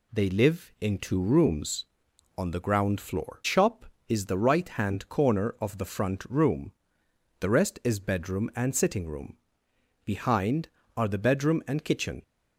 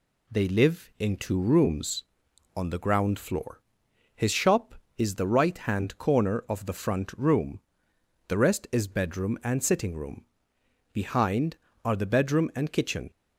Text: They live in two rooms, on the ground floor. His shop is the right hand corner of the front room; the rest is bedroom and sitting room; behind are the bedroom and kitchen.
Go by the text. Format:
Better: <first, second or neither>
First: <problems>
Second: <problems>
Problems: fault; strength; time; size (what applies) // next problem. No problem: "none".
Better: second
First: skips "His"; at 3.4 s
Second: none